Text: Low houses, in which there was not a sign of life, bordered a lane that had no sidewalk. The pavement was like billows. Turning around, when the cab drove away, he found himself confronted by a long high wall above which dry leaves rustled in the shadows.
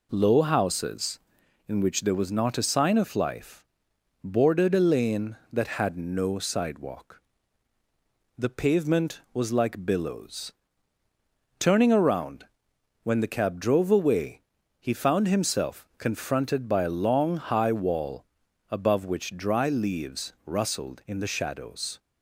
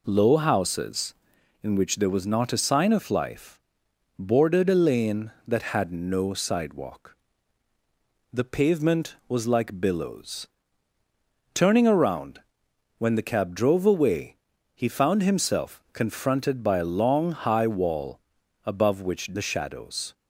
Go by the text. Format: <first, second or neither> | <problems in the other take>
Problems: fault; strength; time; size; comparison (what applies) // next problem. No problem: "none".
first | pauses between "wall" and "above"; at 18.1 s; 0.44 s long; also in the first // skips "dry leaves rustled in"; at 19.3 s